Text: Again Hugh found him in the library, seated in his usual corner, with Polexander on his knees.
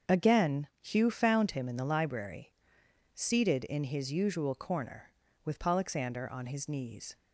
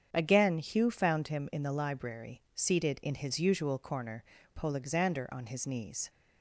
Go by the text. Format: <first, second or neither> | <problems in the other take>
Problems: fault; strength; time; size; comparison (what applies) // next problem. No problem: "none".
first | starts louder than the rest; strong; until 1.1 s; 7.5 dB; also in the first // skips "with"; at 4.3 s